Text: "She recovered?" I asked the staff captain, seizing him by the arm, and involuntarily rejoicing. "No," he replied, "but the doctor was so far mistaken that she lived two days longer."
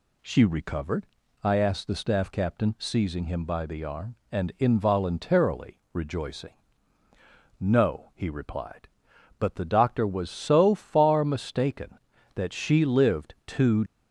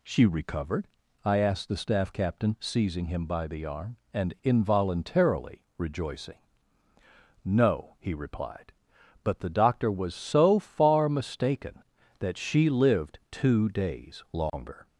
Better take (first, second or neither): second